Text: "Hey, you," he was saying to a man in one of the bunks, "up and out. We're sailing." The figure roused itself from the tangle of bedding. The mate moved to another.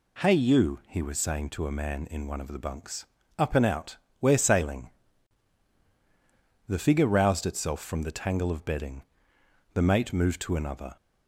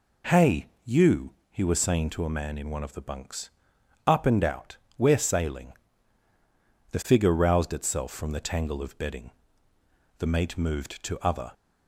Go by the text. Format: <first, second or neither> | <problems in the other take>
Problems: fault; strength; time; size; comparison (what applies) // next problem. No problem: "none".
first | says "other" for "another"; at 11.1 s